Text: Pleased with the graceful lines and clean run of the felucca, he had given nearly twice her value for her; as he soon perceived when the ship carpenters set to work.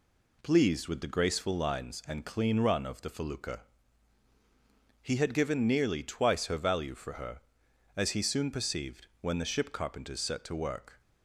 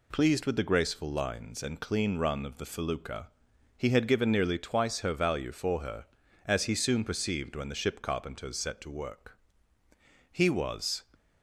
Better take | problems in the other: first | goes on to say "He was"; noticeable; from 10.2 s on; 0.74 s long

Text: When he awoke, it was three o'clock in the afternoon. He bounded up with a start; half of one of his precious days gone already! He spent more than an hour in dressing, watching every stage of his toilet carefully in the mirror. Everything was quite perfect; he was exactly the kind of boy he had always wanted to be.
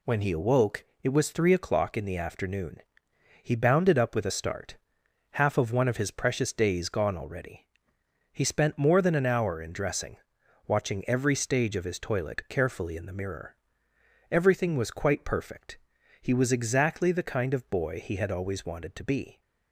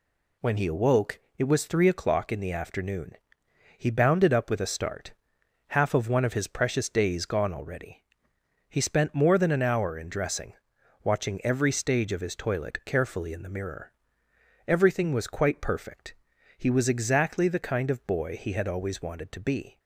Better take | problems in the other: neither | none

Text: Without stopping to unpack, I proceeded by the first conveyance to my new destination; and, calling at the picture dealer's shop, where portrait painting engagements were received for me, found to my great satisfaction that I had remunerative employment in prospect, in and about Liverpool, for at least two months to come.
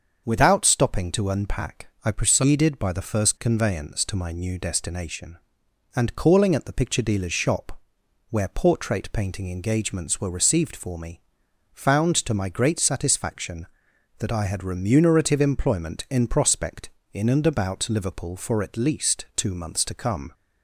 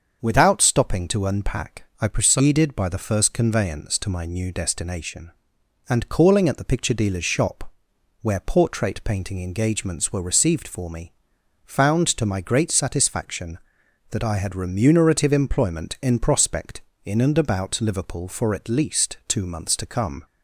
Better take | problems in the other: neither | starts louder than the rest; the same in both

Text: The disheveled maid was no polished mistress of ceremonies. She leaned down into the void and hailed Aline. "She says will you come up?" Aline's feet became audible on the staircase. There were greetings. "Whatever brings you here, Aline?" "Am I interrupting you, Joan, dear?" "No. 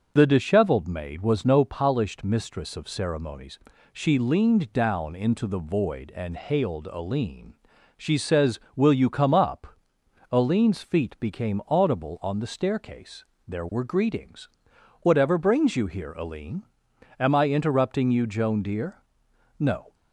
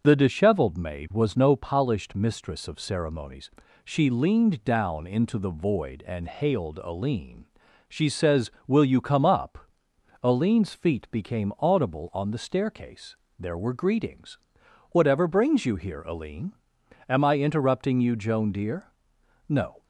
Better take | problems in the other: neither | starts louder than the rest; the same in both

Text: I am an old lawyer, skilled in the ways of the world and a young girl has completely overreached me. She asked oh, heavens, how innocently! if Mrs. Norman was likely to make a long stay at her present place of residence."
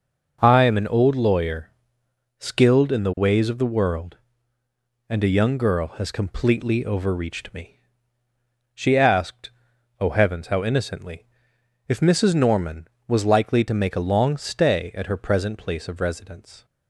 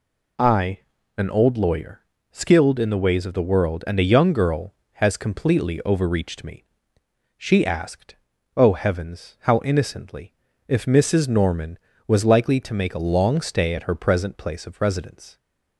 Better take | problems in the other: first | skips "am"; at 0.9 s // pauses between "asked" and "oh"; at 8.1 s; 0.42 s long; noticeable in the first

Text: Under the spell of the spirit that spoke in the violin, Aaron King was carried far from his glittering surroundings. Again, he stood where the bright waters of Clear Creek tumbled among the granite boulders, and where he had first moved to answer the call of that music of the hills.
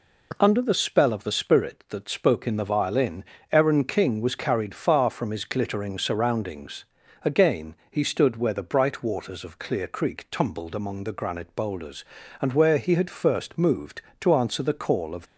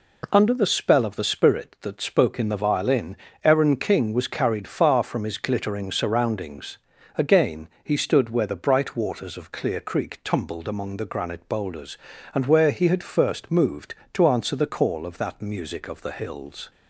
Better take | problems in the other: second | stops before "that music of the hills"; at 15.2 s

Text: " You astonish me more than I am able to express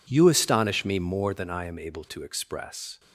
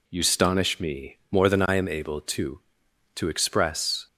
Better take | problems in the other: first | says "to" twice; at 3.1 s

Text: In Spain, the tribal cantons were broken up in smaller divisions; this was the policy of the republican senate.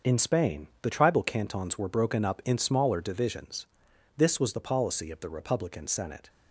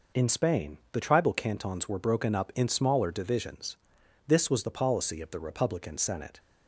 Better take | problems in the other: second | gets quieter; strong; throughout; 8 dB

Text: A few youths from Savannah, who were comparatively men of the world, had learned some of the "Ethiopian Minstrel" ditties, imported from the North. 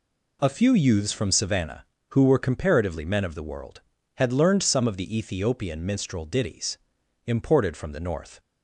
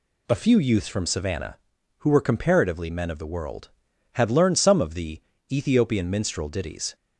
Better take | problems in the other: first | pauses between "the" and "Ethiopian"; slight; at 5.2 s; 0.30 s long // stops before "imported from the North"; at 6.9 s

